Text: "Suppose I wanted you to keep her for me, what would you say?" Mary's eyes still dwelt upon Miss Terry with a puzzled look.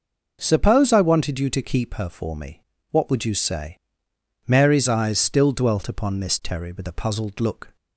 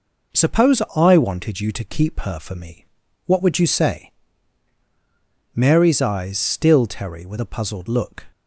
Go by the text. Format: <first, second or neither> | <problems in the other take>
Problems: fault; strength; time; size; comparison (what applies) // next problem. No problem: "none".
first | skips "dwelt upon Miss"; at 6.8 s